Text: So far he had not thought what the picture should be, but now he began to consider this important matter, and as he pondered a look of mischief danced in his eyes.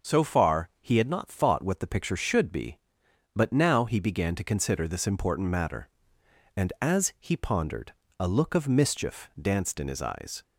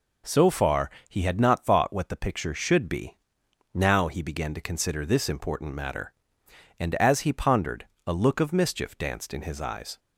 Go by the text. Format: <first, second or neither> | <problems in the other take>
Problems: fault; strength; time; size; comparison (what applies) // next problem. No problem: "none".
first | pauses between "far" and "he"; slight; at 0.8 s; 0.18 s long // skips "but"; at 3.4 s // pauses between "pondered" and "a"; slight; at 7.8 s; 0.22 s long; slight in the first